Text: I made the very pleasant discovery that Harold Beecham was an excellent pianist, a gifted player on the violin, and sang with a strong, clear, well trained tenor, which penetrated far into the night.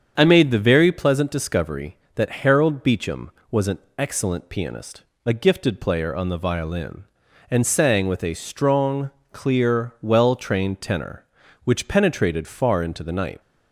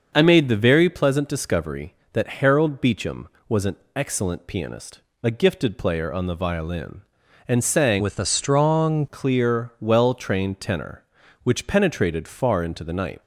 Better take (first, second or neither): first